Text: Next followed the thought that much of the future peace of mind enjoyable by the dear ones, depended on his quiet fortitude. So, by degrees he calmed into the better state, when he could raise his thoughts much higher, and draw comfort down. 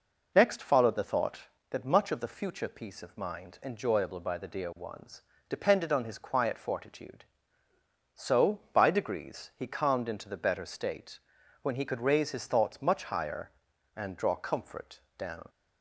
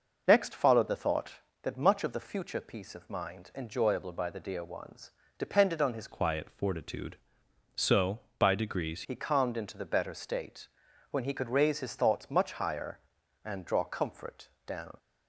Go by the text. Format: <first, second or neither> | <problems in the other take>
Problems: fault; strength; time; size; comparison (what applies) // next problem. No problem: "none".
first | changes voice from "quiet" to "degrees"; from 6.0 to 9.0 s; 3.0 s long // pauses between "comfort" and "down"; slight; at 14.4 s; 0.18 s long; slight in the first